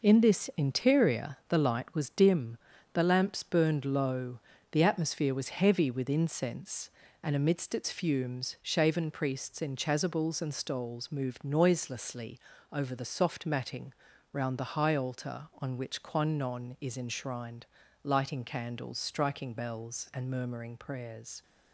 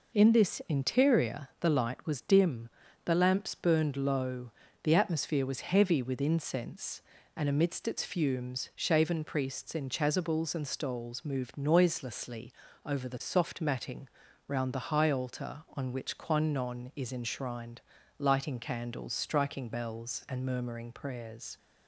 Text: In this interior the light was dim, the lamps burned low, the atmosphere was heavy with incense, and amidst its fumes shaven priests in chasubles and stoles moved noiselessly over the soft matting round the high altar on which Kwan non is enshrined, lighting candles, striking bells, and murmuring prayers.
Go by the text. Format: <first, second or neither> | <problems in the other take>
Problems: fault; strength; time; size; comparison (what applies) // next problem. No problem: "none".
second | gets quieter; strong; throughout; 7 dB // pauses between "noiselessly" and "over"; slight; at 12.3 s; 0.32 s long; slight in the second // pauses between "matting" and "round"; at 13.9 s; 0.40 s long; also in the second